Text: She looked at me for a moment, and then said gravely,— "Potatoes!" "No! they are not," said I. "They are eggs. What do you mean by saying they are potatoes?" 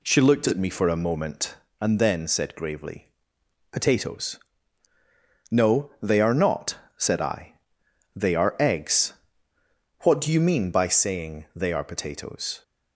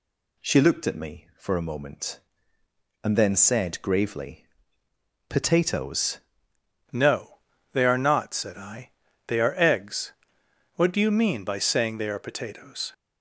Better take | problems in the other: first | changes voice at "No"; from 6.9 s on; 6.0 s long

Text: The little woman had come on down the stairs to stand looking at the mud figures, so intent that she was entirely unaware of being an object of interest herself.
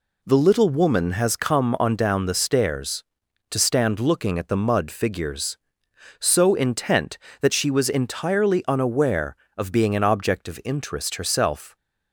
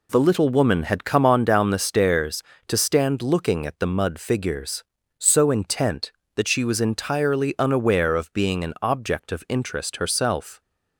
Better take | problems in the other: second | says "has" for "had"; at 1.1 s

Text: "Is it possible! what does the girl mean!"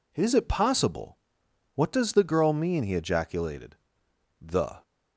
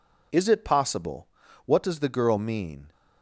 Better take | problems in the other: second | goes on to say "he ejaculated the"; strong; from 2.8 s on; 1.9 s long

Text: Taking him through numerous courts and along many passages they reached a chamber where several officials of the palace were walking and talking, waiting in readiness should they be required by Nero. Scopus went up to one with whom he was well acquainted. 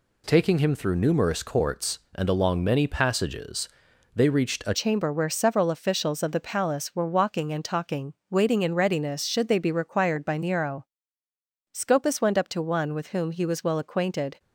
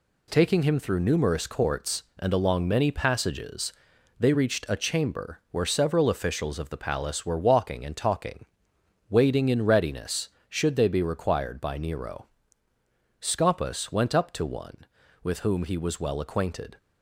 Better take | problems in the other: second | pauses between "passages" and "they"; noticeable; at 3.6 s; 0.46 s long; noticeable in the second // changes voice at "chamber"; from 4.7 s on; 9.6 s long

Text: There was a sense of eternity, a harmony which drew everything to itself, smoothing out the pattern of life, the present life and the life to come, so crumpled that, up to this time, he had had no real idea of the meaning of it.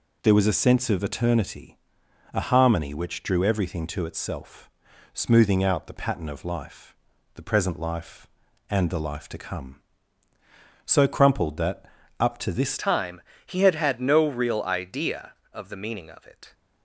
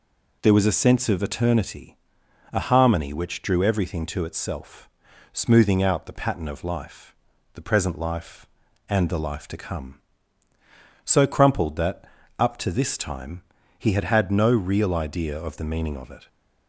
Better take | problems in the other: second | changes voice at "time"; from 12.7 s on; 3.8 s long

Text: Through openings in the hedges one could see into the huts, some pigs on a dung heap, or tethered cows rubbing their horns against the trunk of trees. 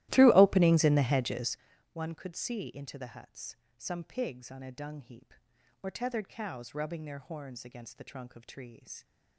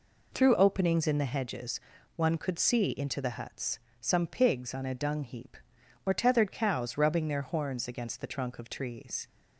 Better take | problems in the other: second | starts louder than the rest; strong; until 1.6 s; 15.5 dB // pauses between "hedges" and "one"; at 1.5 s; 0.38 s long; also in the second

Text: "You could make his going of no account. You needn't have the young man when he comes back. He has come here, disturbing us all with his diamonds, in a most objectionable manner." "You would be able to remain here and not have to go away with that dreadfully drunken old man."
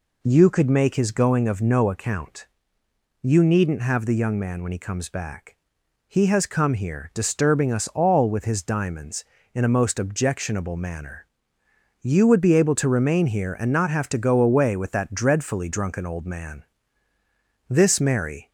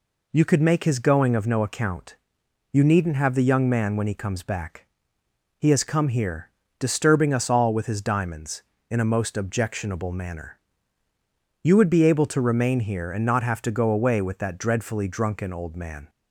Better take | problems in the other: second | goes on to say "This Mary"; noticeable; from 17.6 s on; 0.82 s long

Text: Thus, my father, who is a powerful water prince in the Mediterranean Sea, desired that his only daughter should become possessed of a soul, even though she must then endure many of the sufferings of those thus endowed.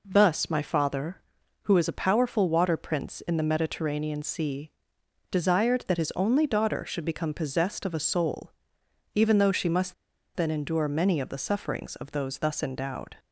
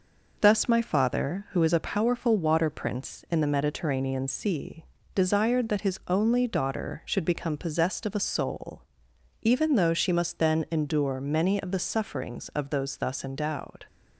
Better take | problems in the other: second | pauses between "must" and "then"; at 9.9 s; 0.41 s long

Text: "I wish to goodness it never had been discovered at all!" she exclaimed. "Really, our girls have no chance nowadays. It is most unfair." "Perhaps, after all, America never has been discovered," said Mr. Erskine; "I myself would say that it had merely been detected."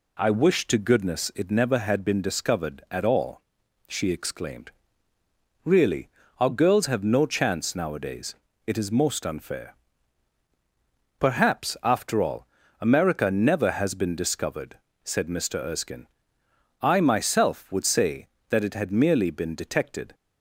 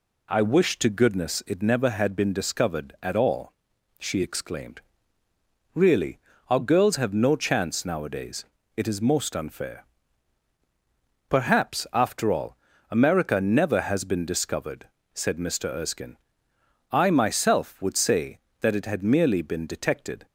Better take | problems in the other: neither | none

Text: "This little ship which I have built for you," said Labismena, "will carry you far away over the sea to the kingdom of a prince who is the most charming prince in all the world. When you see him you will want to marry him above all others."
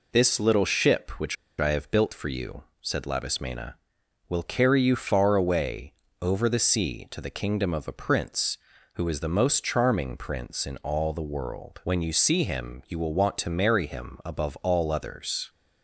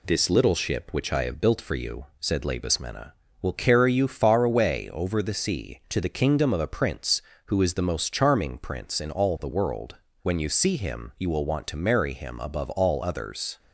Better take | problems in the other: second | pauses between "which" and "I"; slight; at 1.3 s; 0.24 s long // pauses between "away" and "over"; slight; at 5.9 s; 0.28 s long

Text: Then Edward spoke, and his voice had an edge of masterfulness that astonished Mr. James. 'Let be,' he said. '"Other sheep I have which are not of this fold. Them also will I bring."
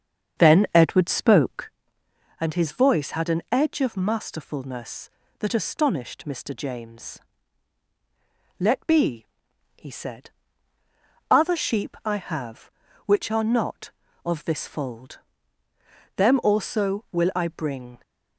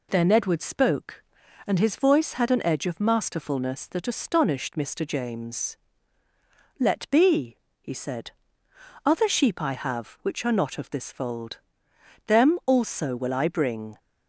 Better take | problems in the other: second | starts louder than the rest; strong; until 1.8 s; 7.5 dB

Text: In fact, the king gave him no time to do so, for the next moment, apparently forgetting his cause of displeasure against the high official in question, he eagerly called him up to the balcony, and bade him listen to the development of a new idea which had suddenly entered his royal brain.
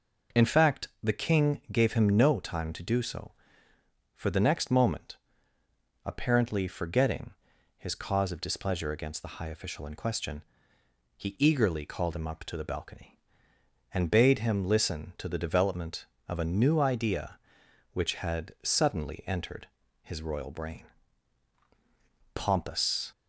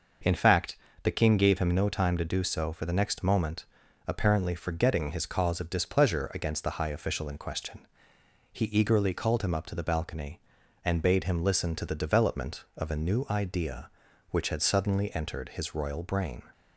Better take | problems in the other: second | pauses between "forgetting" and "his"; at 7.3 s; 0.44 s long // pauses between "entered" and "his"; slight; at 19.6 s; 0.36 s long // goes on to say "Pompous"; noticeable; from 22.3 s on; 0.78 s long

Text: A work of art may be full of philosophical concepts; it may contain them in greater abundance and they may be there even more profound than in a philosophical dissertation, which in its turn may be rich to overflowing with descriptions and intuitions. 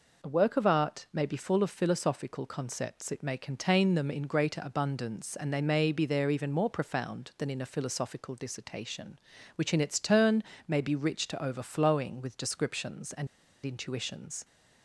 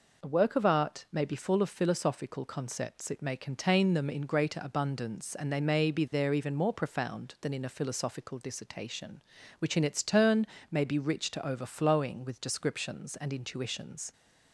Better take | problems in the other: second | pauses between "turn" and "may"; slight; at 10.4 s; 0.24 s long; slight in the second // pauses between "and" and "intuitions"; at 13.2 s; 0.37 s long

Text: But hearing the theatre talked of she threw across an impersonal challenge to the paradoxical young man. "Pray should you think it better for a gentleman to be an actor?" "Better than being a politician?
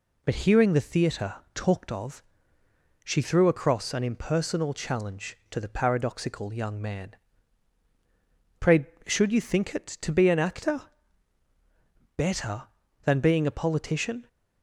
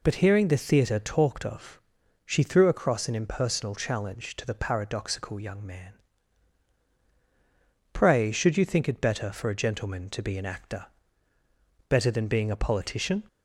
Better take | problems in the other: second | pauses between "theatre" and "talked"; slight; at 1.3 s; 0.18 s long // pauses between "of" and "she"; noticeable; at 2.2 s; 0.82 s long; noticeable in the second // skips "better for a gentleman"; at 9.8 s

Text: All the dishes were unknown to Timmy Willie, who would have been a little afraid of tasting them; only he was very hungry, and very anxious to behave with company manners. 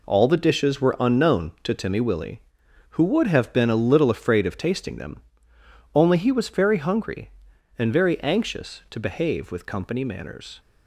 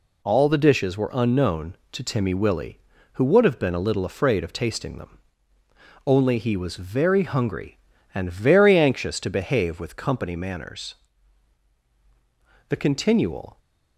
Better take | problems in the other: first | goes on to say "The continual"; noticeable; from 12.6 s on; 0.90 s long

